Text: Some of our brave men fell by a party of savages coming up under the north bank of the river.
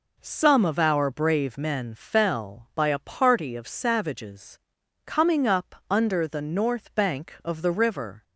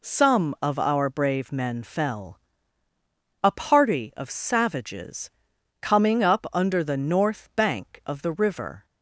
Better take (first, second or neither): first